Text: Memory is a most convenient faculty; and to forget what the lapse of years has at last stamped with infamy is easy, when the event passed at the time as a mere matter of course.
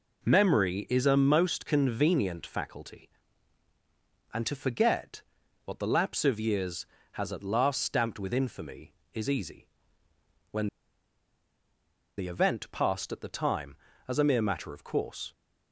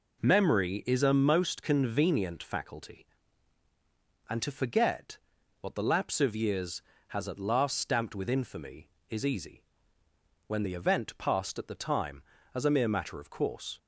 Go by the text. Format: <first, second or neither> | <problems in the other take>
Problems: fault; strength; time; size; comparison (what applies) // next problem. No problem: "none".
second | pauses between "forget" and "what"; at 5.2 s; 0.44 s long; also in the second // pauses between "when" and "the"; strong; at 10.6 s; 1.4 s long